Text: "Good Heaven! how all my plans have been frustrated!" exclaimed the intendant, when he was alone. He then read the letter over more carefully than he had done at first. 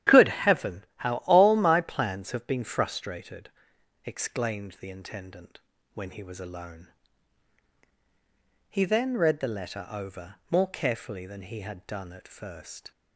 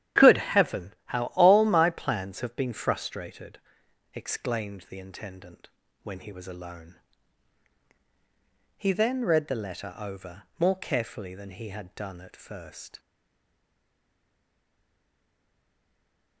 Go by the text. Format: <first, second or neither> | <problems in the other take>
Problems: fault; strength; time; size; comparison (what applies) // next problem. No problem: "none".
first | starts louder than the rest; strong; until 1.3 s; 10.5 dB; strong in the first // stays silent after the last word; strong; from 12.9 s on; 3.5 s long